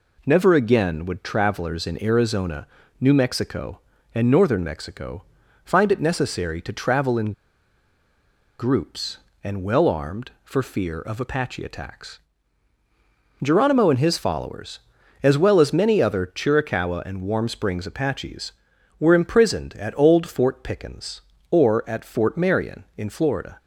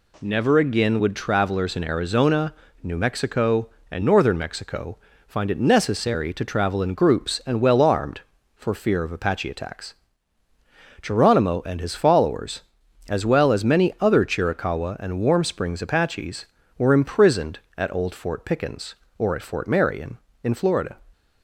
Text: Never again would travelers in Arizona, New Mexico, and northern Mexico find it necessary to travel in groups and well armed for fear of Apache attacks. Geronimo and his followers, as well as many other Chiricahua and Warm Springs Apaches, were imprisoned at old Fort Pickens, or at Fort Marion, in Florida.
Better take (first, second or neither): second